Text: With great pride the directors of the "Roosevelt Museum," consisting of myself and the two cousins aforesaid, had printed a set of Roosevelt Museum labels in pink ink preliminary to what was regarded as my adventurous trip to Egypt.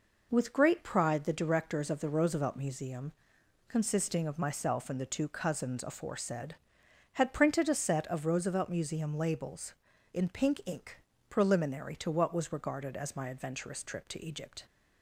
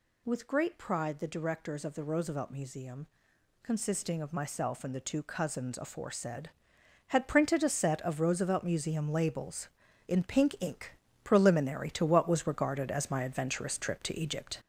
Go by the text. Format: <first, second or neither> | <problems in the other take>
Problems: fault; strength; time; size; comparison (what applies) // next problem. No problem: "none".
first | gets louder; noticeable; throughout; 5 dB // pauses between "ink" and "preliminary"; slight; at 10.9 s; 0.30 s long; slight in the first